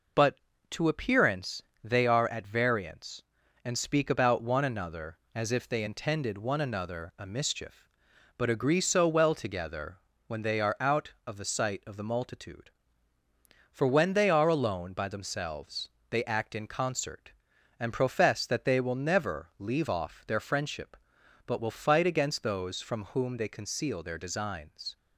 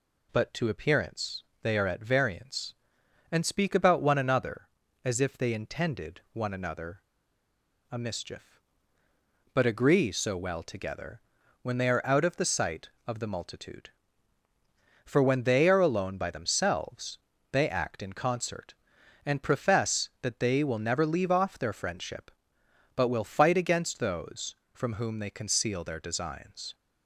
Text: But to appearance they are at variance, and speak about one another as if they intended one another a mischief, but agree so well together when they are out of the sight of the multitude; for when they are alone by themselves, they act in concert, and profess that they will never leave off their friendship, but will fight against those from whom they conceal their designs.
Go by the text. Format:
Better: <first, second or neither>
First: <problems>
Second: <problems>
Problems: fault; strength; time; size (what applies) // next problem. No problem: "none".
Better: first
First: pauses between "appearance" and "they"; slight; at 1.6 s; 0.22 s long // pauses between "together" and "when"; slight; at 9.9 s; 0.26 s long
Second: pauses between "appearance" and "they"; slight; at 1.4 s; 0.18 s long // pauses between "another" and "a"; noticeable; at 7.0 s; 0.89 s long // pauses between "together" and "when"; at 11.2 s; 0.42 s long